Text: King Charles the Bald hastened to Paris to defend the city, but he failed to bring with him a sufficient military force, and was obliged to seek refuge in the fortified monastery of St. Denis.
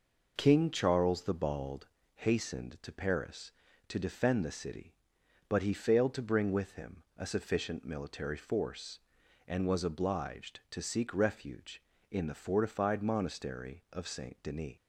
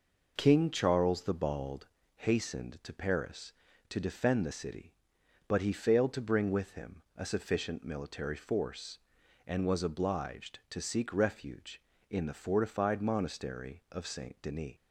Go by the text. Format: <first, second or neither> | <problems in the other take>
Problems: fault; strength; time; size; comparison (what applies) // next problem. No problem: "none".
neither | pauses between "Bald" and "hastened"; slight; the same in both